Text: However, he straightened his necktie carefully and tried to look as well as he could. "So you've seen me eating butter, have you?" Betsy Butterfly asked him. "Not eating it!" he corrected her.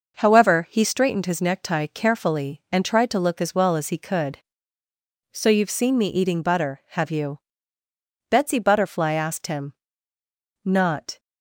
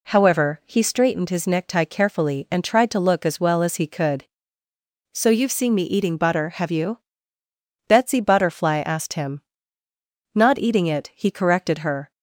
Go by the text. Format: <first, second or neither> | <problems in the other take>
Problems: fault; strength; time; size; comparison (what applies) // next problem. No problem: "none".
second | stops before "eating it he corrected her"; at 11.1 s